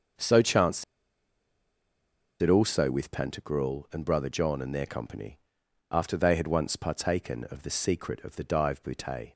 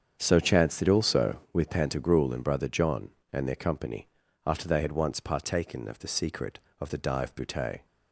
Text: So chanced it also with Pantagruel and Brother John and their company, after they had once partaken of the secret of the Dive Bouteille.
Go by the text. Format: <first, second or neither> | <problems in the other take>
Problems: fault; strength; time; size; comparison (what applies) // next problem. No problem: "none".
second | starts louder than the rest; until 2.7 s; 6.5 dB; strong in the second // pauses between "chanced" and "it"; strong; at 0.8 s; 1.5 s long